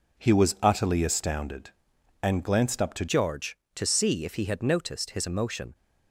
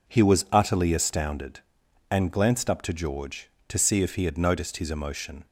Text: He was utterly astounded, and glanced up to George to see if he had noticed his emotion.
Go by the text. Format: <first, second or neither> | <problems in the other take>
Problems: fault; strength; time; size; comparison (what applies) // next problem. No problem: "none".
second | changes voice at "George"; from 3.0 s on; 2.7 s long